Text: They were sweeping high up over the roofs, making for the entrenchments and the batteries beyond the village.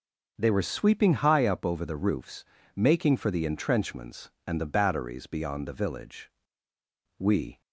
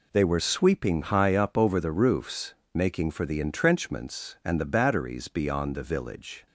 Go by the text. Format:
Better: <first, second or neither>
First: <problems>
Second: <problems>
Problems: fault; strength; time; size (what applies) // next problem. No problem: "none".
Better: second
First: goes on to say "We"; slight; from 7.1 s on; 0.42 s long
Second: none